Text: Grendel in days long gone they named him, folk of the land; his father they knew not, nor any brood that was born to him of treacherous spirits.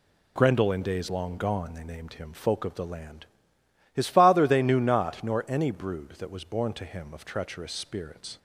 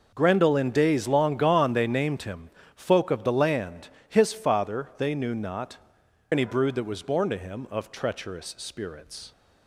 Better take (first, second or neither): first